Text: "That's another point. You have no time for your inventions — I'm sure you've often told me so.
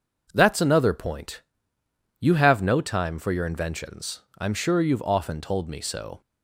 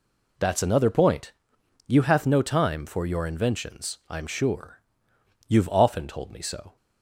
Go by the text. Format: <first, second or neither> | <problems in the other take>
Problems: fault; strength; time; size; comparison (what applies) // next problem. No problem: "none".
first | says "hath" for "have"; at 2.0 s // pauses between "sure" and "you've"; noticeable; at 4.8 s; 0.66 s long